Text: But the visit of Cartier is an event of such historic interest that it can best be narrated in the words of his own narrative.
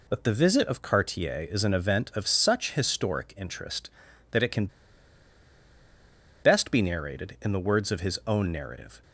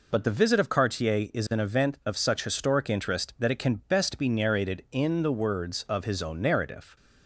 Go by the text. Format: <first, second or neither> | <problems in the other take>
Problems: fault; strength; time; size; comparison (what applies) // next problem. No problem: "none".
second | pauses between "can" and "best"; strong; at 4.6 s; 1.7 s long